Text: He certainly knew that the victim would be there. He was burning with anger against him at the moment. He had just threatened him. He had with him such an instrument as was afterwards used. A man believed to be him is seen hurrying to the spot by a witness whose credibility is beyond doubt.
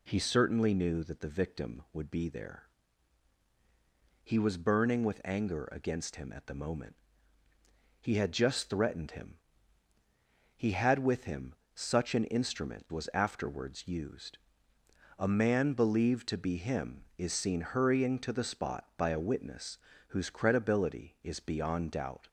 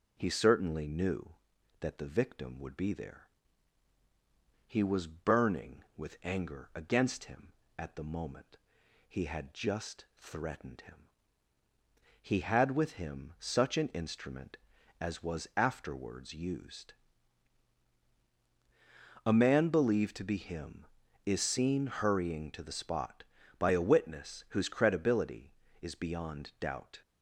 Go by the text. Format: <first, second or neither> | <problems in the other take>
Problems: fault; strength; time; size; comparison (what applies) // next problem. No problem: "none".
second | pauses between "him" and "such"; slight; at 11.5 s; 0.20 s long // skips "as"; at 12.8 s // pauses between "witness" and "whose"; slight; at 19.7 s; 0.32 s long